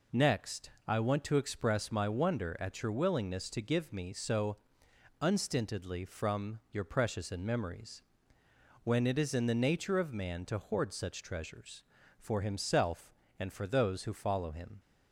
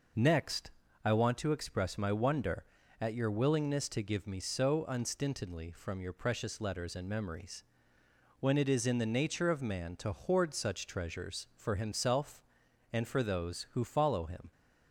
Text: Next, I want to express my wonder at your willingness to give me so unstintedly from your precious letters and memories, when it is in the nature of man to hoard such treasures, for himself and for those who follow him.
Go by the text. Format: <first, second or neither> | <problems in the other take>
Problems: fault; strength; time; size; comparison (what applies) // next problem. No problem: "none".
second | pauses between "so" and "unstintedly"; noticeable; at 4.5 s; 0.66 s long // skips "letters"; at 7.2 s